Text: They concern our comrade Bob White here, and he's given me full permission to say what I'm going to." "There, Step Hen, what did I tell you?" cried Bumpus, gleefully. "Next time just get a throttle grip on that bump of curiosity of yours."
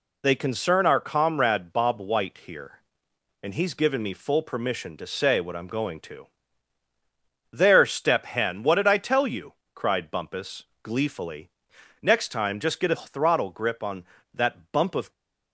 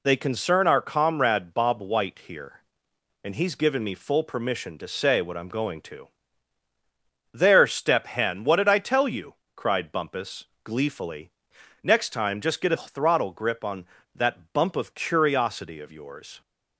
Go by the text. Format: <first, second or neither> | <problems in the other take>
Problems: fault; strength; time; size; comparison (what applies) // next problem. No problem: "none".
second | stops before "curiosity of yours"; at 15.1 s